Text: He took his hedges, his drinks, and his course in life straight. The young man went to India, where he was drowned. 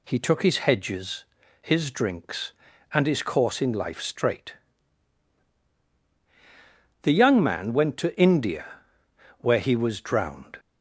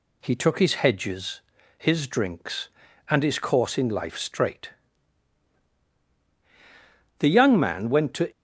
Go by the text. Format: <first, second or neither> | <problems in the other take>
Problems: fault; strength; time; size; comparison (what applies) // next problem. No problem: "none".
first | stops before "India where he was drowned"; at 8.3 s